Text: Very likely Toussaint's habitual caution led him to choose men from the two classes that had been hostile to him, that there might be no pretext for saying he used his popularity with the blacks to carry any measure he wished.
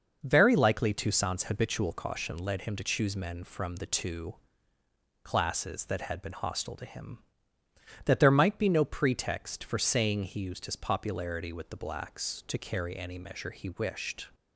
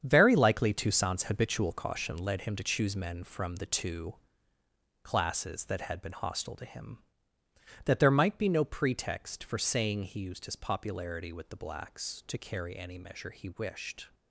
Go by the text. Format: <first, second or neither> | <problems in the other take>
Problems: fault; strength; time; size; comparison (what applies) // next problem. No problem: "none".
first | gets quieter; strong; throughout; 9.5 dB // pauses between "two" and "classes"; noticeable; at 4.1 s; 0.88 s long; noticeable in the first